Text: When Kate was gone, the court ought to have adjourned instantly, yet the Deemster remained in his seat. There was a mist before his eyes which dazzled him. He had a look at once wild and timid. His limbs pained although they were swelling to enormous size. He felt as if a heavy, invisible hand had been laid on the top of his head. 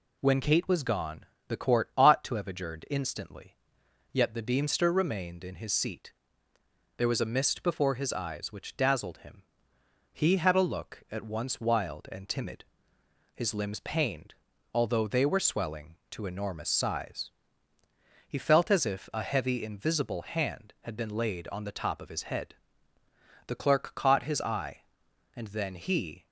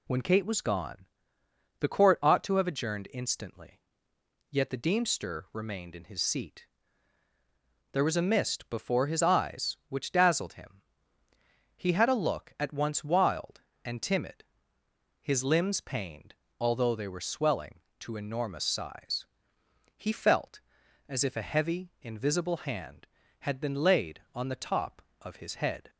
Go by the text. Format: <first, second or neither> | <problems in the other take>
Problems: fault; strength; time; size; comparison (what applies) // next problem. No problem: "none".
second | pauses between "pained" and "although"; at 14.3 s; 0.40 s long; slight in the second // goes on to say "The clerk caught his eye and then he"; strong; from 23.4 s on; 2.8 s long